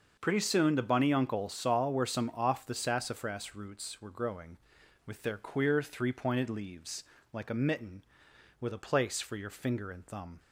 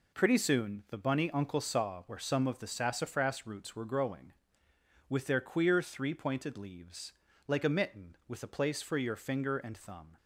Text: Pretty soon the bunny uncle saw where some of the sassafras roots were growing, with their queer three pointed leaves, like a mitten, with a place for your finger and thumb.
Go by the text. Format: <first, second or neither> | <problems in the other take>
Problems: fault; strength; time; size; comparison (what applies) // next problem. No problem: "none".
second | starts louder than the rest; until 1.2 s; 6.5 dB // says "off" for "of"; at 2.3 s